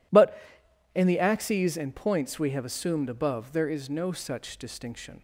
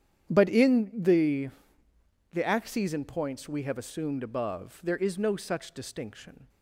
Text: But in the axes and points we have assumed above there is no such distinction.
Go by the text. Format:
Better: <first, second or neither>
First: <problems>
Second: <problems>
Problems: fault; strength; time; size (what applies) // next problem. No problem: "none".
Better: first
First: none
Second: starts louder than the rest; strong; until 1.3 s; 9 dB // says "the" twice; at 2.3 s